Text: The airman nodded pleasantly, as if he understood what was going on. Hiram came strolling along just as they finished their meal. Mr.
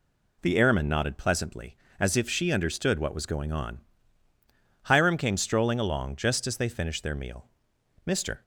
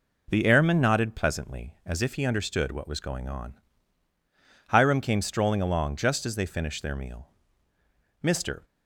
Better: second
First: says "she" for "he"; at 2.2 s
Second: none

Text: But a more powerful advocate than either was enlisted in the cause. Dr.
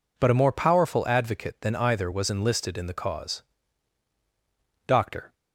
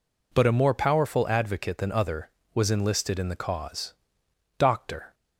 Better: first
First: none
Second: says "other" for "either"; at 1.9 s

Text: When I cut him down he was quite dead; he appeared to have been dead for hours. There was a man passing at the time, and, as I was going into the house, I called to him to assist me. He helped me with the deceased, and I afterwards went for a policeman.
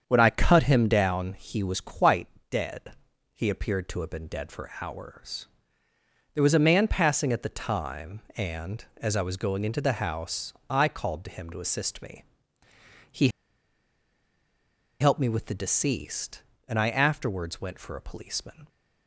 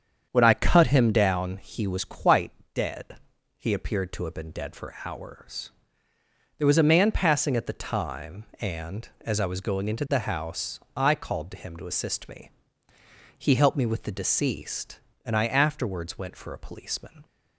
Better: second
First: starts louder than the rest; strong; until 1.0 s; 7.5 dB // pauses between "quite" and "dead"; slight; at 2.2 s; 0.22 s long // pauses between "He" and "helped"; strong; at 13.2 s; 1.7 s long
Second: starts louder than the rest; strong; until 1.3 s; 7.5 dB // pauses between "quite" and "dead"; slight; at 2.5 s; 0.22 s long

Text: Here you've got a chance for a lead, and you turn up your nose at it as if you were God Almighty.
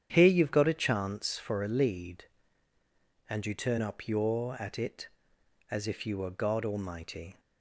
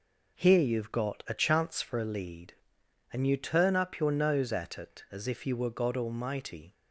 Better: second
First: starts louder than the rest; strong; until 1.1 s; 9 dB // skips "nose"; at 4.5 s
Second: none

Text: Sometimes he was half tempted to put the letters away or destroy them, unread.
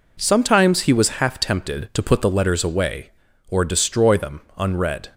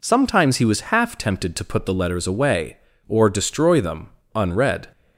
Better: neither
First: none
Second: none

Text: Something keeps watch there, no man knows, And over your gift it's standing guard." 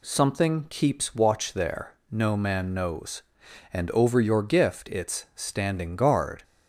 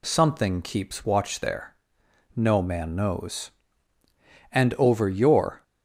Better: first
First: none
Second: stops before "gift it's standing guard"; at 5.6 s

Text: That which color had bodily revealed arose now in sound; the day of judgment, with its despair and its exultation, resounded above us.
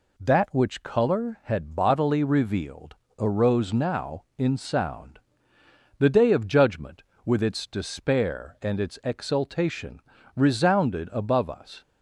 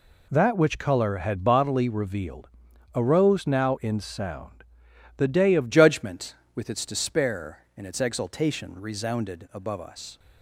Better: first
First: pauses between "revealed" and "arose"; slight; at 2.9 s; 0.24 s long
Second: pauses between "revealed" and "arose"; noticeable; at 2.4 s; 0.46 s long // changes voice at "judgment"; from 5.7 s on; 4.4 s long

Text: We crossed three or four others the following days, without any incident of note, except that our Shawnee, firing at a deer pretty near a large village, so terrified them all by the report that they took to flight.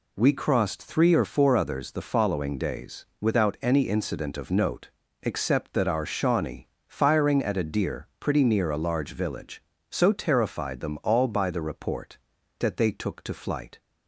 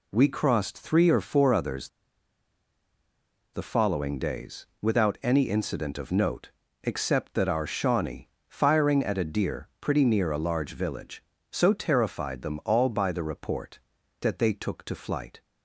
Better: first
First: none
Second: pauses between "others" and "the"; strong; at 1.8 s; 1.6 s long

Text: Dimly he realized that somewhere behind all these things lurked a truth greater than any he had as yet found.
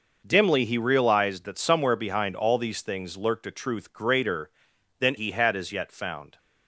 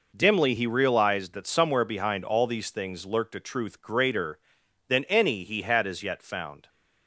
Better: second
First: skips "any"; at 5.1 s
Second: none

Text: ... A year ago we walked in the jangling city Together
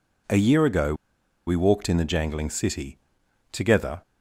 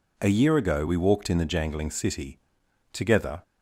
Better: second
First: pauses between "ago" and "we"; noticeable; at 0.9 s; 0.52 s long // pauses between "city" and "Together"; noticeable; at 2.9 s; 0.56 s long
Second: pauses between "city" and "Together"; noticeable; at 2.3 s; 0.56 s long

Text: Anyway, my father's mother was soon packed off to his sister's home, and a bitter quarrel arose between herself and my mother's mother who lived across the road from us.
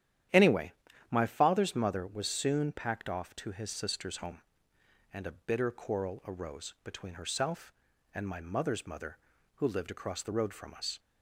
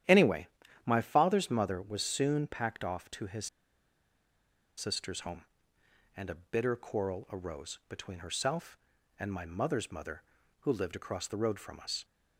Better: first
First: starts louder than the rest; strong; until 1.6 s; 11 dB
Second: starts louder than the rest; strong; until 1.4 s; 11 dB // pauses between "his" and "sister's"; strong; at 3.4 s; 1.3 s long

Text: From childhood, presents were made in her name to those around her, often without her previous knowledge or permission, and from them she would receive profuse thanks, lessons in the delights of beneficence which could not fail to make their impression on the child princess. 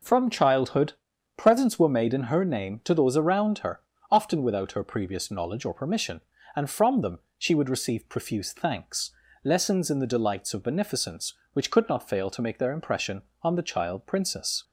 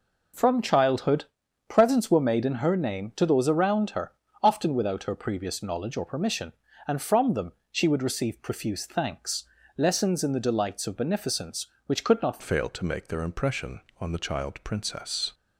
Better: first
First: pauses between "them" and "she"; slight; at 7.1 s; 0.18 s long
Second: pauses between "them" and "she"; slight; at 7.5 s; 0.18 s long // changes voice at "fail"; from 12.4 s on; 2.9 s long

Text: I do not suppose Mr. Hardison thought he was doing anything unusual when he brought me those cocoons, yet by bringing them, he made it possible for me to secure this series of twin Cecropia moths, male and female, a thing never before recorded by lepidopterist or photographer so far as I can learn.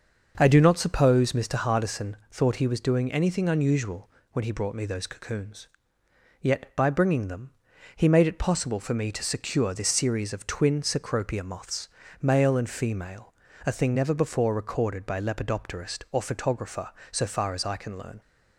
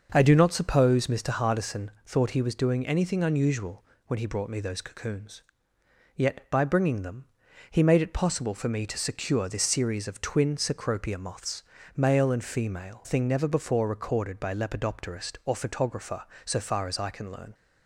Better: first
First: starts louder than the rest; until 1.3 s; 6.5 dB // pauses between "unusual" and "when"; slight; at 4.0 s; 0.24 s long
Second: starts louder than the rest; until 1.1 s; 6.5 dB // pauses between "unusual" and "when"; slight; at 3.8 s; 0.24 s long // skips "a"; at 13.0 s

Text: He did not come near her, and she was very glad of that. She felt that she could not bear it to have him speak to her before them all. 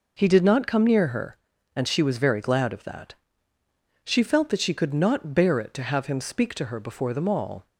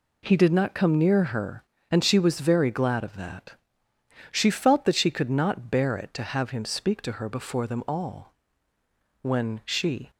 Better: first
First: none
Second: goes on to say "When she"; noticeable; from 9.2 s on; 0.88 s long

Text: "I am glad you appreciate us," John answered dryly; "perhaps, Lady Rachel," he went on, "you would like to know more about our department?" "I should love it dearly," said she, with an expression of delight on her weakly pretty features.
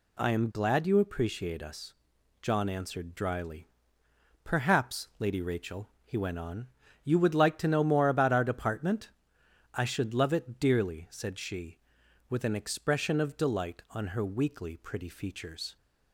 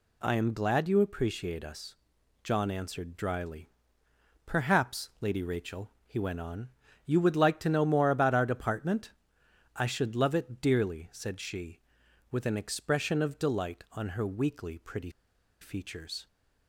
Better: first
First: none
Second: pauses between "pretty" and "features"; noticeable; at 15.0 s; 0.51 s long

